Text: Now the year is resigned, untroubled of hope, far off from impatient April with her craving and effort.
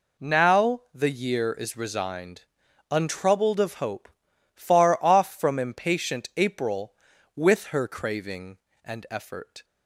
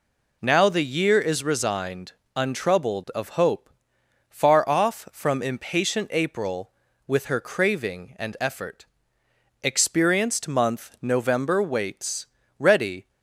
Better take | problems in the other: first | goes on to say "Experienced month November waits ready"; strong; from 9.6 s on; 3.4 s long

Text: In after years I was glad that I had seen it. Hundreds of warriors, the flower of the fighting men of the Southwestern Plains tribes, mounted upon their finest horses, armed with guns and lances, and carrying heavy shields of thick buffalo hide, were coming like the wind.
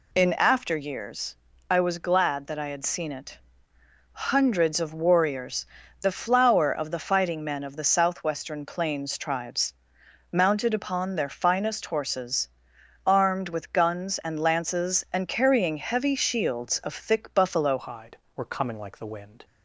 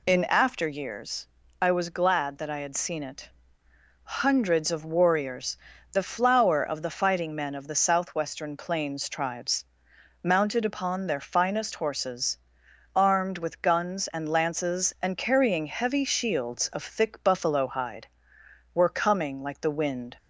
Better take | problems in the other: second | pauses between "years" and "I"; slight; at 1.3 s; 0.32 s long; slight in the second // changes voice at "hide"; from 17.7 s on; 1.7 s long

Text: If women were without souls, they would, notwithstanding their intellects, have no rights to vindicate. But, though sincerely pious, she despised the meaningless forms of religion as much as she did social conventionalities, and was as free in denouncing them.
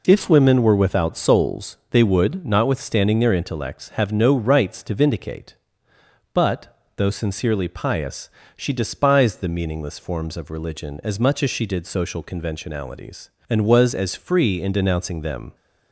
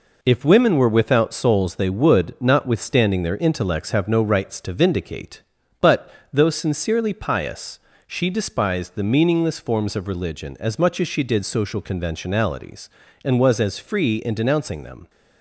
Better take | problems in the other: neither | none

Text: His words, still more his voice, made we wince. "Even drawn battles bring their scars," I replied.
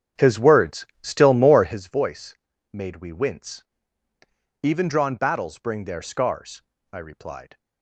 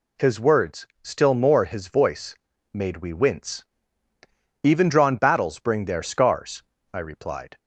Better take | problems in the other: second | starts louder than the rest; strong; until 1.8 s; 9 dB

